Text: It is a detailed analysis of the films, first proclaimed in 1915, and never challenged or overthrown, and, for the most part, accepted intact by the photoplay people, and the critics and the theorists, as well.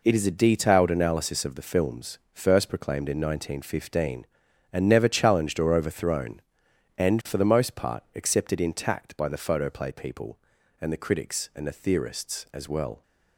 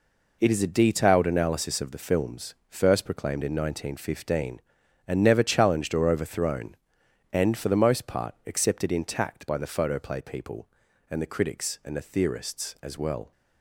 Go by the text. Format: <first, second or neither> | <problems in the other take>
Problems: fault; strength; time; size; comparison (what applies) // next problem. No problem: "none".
neither | none